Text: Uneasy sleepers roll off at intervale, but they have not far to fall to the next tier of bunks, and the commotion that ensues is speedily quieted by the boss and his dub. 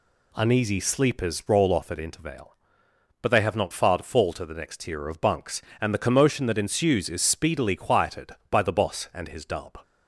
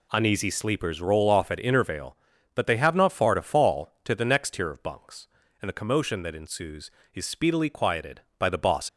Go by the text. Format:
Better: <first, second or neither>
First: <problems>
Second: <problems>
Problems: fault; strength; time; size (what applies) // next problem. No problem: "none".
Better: first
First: none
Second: stops before "and his dub"; at 8.8 s